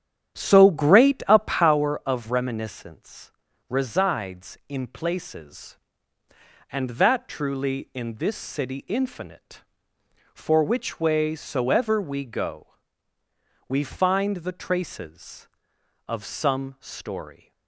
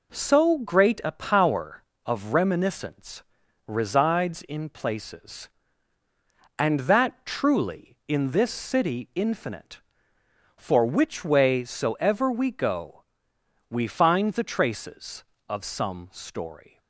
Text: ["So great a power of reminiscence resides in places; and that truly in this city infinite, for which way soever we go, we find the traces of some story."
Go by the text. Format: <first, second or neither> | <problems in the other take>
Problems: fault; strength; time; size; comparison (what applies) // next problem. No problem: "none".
second | starts louder than the rest; strong; until 1.8 s; 10 dB // pauses between "reminiscence" and "resides"; at 3.2 s; 0.40 s long; also in the second